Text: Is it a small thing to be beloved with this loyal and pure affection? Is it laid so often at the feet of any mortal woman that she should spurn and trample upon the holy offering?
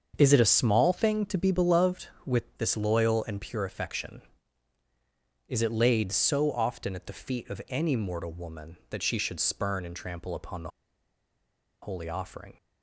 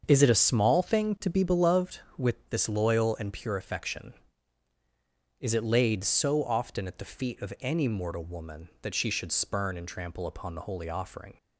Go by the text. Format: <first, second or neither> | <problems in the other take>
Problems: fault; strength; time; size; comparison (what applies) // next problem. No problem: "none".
second | starts louder than the rest; until 1.1 s; 7 dB; also in the second // pauses between "the" and "holy"; at 10.6 s; 1.1 s long